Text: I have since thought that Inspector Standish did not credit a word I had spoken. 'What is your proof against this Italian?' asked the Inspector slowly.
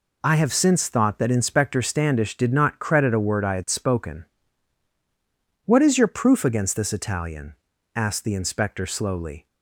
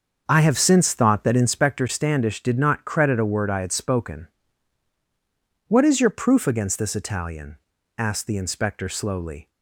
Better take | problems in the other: first | starts louder than the rest; until 1.7 s; 6.5 dB

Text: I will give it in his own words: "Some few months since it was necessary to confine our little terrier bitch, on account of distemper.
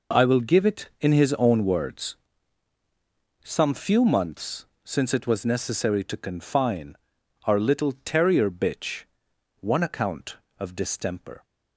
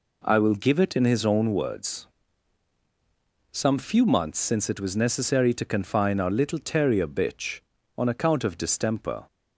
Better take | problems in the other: second | pauses between "months" and "since"; slight; at 4.6 s; 0.18 s long // pauses between "confine" and "our"; noticeable; at 6.9 s; 0.50 s long // says "one" for "on"; at 9.6 s

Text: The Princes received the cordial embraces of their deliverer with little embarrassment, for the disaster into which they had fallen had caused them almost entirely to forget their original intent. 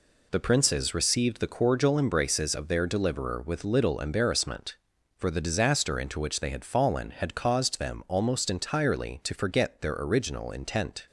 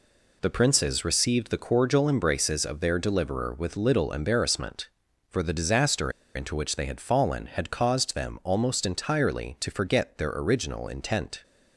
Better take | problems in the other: first | pauses between "disaster" and "into"; slight; at 6.1 s; 0.24 s long

